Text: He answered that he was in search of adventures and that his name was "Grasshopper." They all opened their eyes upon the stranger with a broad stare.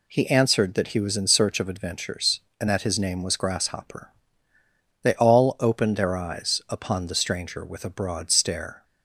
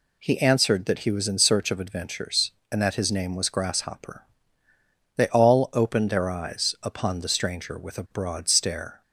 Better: neither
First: none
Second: none

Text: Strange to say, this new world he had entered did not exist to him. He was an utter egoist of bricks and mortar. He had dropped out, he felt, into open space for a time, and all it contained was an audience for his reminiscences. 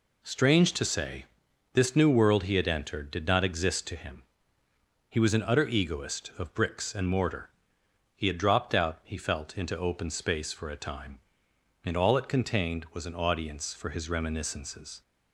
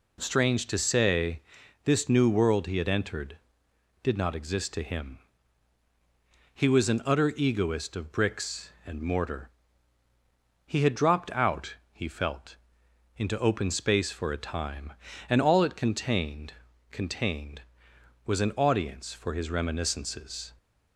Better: first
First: none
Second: says "contained" twice; at 16.9 s

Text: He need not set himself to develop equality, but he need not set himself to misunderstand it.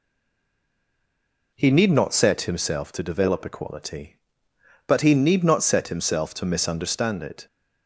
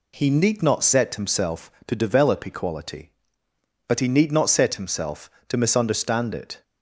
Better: second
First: stays silent before the first word; noticeable; until 1.5 s; 1.5 s long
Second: none

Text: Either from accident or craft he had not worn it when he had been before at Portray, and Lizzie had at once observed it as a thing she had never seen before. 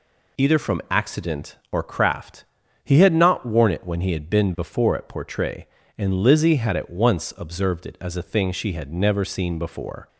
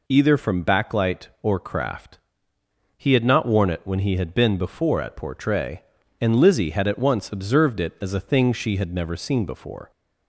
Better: first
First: pauses between "craft" and "he"; at 2.4 s; 0.40 s long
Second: says "backlight" for "accident"; at 0.6 s // pauses between "craft" and "he"; noticeable; at 2.1 s; 0.80 s long

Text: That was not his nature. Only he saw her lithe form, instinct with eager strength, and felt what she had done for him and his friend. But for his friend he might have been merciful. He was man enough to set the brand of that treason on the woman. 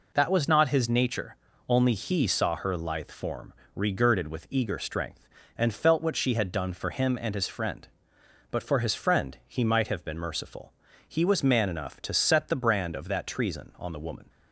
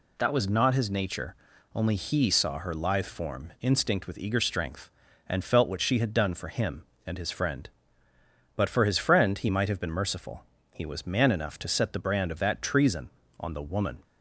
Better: second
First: says "regirded" for "instinct"; at 3.7 s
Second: none

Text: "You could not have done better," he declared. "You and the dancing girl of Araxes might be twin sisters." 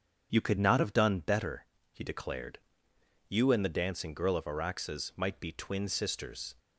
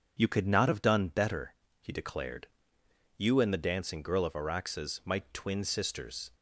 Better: first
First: starts louder than the rest; strong; until 1.3 s; 8 dB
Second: starts louder than the rest; strong; until 1.2 s; 7 dB // skips "be"; at 5.2 s

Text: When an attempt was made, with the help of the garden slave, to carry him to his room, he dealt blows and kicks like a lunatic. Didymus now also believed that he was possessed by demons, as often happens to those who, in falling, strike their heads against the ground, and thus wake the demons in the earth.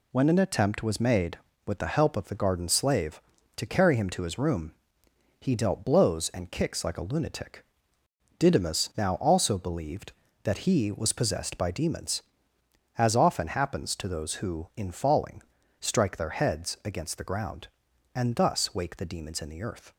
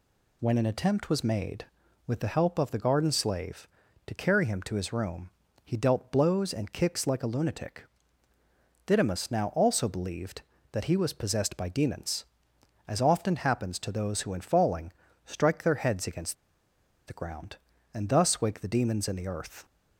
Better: first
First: none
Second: pauses between "against" and "the"; noticeable; at 16.3 s; 0.74 s long

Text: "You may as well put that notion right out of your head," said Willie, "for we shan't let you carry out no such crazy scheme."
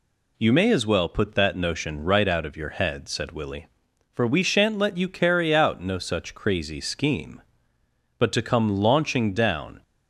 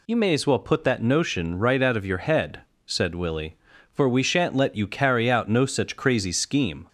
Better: second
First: goes on to say "But to come launching down"; from 8.1 s on; 1.6 s long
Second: none

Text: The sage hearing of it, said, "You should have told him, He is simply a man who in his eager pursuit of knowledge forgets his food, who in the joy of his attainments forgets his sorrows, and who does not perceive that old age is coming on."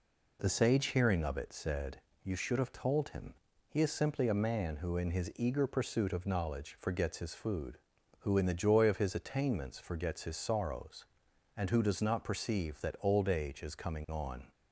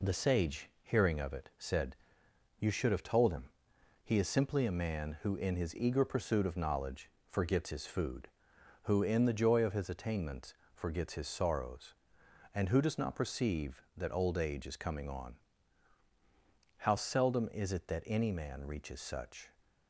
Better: first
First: none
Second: pauses between "knowledge" and "forgets"; slight; at 7.0 s; 0.20 s long // pauses between "attainments" and "forgets"; slight; at 10.5 s; 0.18 s long // goes on to say "How seldom is it that any man reaches such"; strong; from 16.7 s on; 2.7 s long

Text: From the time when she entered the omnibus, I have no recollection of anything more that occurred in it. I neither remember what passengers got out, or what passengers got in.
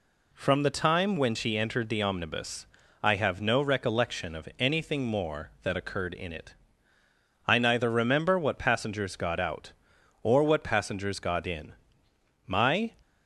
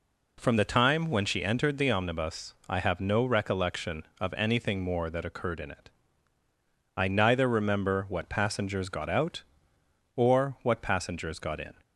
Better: second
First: goes on to say "My"; slight; from 12.4 s on; 0.46 s long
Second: none

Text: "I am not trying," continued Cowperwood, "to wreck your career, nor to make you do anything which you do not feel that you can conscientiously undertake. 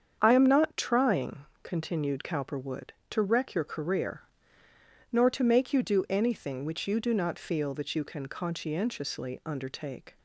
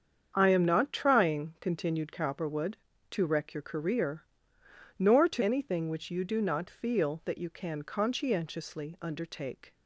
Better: first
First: starts louder than the rest; strong; until 1.2 s; 7.5 dB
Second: starts louder than the rest; strong; until 1.3 s; 7.5 dB // skips "make you do"; at 5.4 s

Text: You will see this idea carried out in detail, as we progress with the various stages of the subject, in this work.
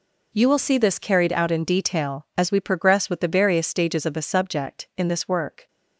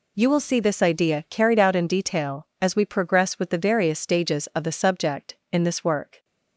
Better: second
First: skips "idea"; at 0.9 s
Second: none

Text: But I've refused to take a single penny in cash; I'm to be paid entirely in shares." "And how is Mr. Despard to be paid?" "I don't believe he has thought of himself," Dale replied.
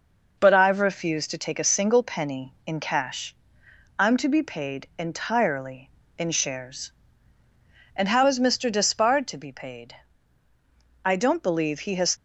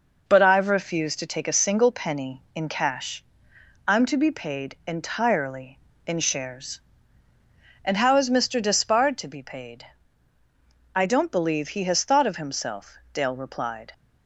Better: second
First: stops before "thought of himself Dale replied"; at 12.1 s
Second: none

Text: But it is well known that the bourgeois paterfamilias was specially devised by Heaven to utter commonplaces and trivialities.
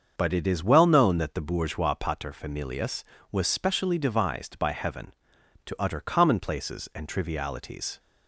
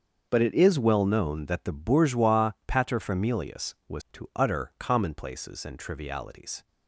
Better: first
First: starts louder than the rest; until 1.1 s; 6.5 dB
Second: starts louder than the rest; until 1.3 s; 6.5 dB // pauses between "bourgeois" and "paterfamilias"; slight; at 2.5 s; 0.16 s long // skips "specially devised by Heaven"; at 4.0 s

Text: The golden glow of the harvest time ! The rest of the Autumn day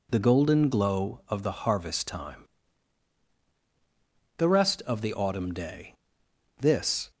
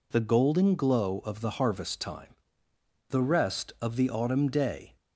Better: second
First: goes on to say "This"; from 6.5 s on; 0.52 s long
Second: none

